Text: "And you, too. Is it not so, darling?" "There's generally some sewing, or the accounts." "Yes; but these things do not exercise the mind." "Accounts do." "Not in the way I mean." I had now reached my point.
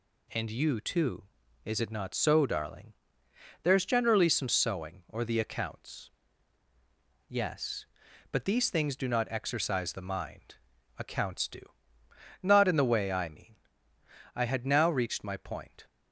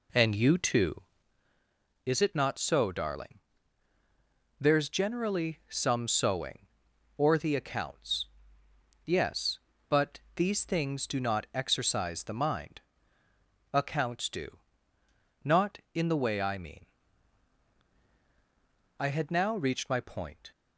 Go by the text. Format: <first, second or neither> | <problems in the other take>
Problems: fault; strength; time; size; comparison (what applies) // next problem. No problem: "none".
first | starts louder than the rest; slight; until 1.3 s; 2.5 dB // pauses between "but" and "these"; slight; at 10.1 s; 0.16 s long